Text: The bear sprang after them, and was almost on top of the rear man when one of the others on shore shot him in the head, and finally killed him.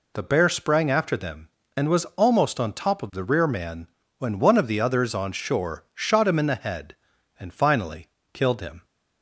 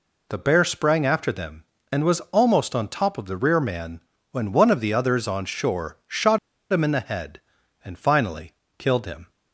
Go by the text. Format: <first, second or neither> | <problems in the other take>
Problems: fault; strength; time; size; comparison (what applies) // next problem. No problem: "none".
first | pauses between "man" and "when"; slight; at 4.0 s; 0.30 s long; slight in the first // pauses between "shot" and "him"; slight; at 6.3 s; 0.35 s long // pauses between "finally" and "killed"; slight; at 8.5 s; 0.26 s long; slight in the first